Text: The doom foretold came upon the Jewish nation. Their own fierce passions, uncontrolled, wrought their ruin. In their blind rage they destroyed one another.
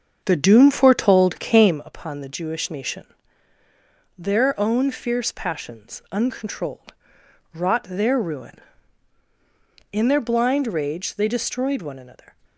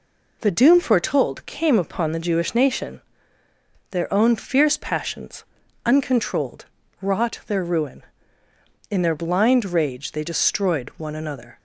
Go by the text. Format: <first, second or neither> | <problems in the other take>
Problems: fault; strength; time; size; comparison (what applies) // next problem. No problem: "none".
second | starts louder than the rest; until 1.8 s; 7 dB